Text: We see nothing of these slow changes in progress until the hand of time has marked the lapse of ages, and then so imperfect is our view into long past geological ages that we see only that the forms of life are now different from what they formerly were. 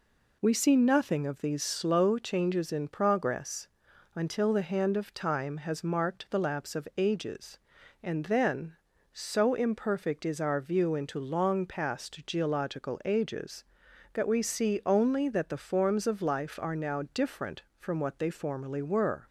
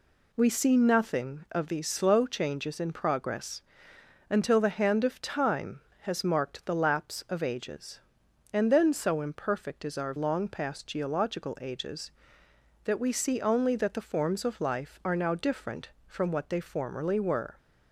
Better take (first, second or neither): first